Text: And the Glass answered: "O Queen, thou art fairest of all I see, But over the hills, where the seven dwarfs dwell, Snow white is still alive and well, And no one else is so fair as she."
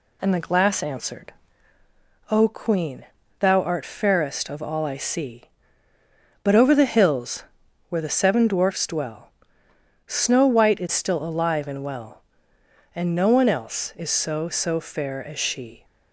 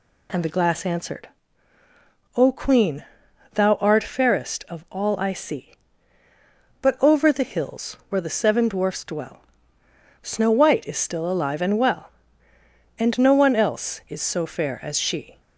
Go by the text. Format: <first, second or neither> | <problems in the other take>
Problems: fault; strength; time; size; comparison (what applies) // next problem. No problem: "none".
second | says "so" twice; at 14.4 s